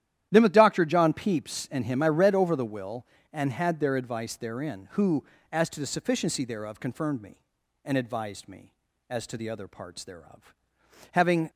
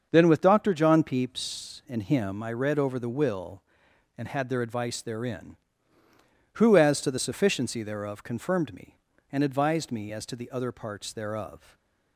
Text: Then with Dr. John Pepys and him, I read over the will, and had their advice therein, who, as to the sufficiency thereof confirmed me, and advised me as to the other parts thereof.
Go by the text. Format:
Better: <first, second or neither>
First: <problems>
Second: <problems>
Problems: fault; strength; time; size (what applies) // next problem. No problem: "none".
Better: second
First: starts louder than the rest; strong; until 1.3 s; 11.5 dB // goes on to say "Having"; slight; from 11.1 s on; 0.38 s long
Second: starts louder than the rest; until 1.1 s; 6.5 dB